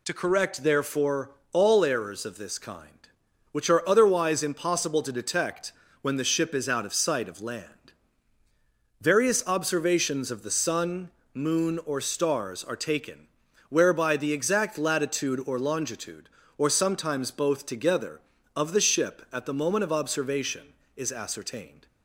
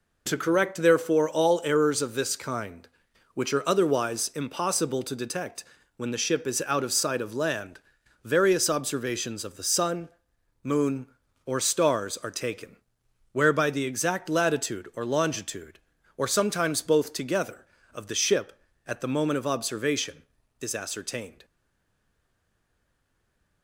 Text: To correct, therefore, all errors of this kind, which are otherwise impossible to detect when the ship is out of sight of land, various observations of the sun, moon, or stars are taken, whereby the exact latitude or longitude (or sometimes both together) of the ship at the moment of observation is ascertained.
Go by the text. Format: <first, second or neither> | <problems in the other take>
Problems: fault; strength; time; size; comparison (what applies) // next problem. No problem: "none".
first | pauses between "detect" and "when"; slight; at 5.6 s; 0.32 s long; slight in the first // stays silent after the last word; from 21.4 s on; 2.2 s long